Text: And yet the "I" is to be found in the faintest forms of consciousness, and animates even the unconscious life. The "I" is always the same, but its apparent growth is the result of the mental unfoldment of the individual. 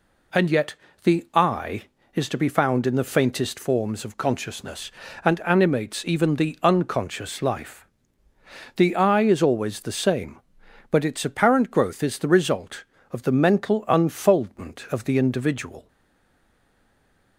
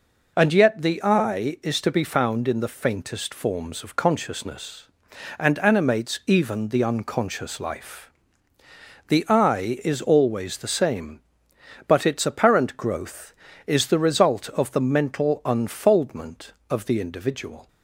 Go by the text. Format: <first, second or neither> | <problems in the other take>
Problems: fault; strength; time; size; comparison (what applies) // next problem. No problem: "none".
second | pauses between "yet" and "the"; slight; at 0.7 s; 0.28 s long // stays silent after the last word; noticeable; from 15.8 s on; 1.5 s long